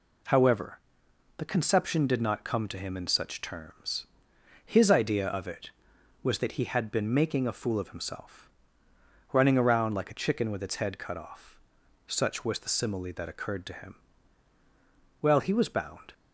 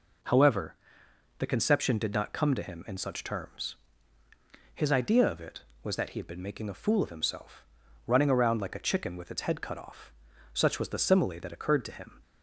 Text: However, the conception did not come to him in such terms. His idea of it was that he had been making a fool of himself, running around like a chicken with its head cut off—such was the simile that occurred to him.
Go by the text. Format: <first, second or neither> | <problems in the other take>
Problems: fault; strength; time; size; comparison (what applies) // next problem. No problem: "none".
second | goes on to say "Well he was bound"; noticeable; from 15.2 s on; 0.92 s long